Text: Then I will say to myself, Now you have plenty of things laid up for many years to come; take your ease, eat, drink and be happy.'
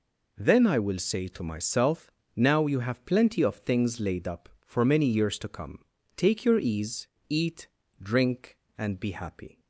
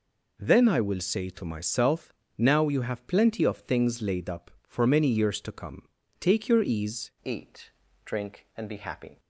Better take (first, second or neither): first